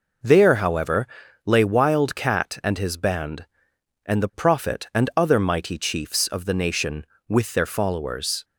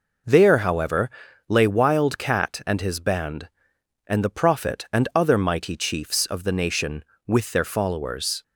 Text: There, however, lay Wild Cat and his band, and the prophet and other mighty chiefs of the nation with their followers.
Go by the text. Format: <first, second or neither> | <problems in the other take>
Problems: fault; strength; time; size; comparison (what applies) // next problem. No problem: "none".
neither | none